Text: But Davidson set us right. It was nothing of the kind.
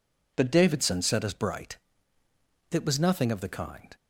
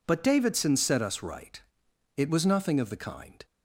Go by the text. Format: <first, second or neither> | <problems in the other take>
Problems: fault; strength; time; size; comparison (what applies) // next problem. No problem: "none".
second | says "bright" for "right"; at 1.3 s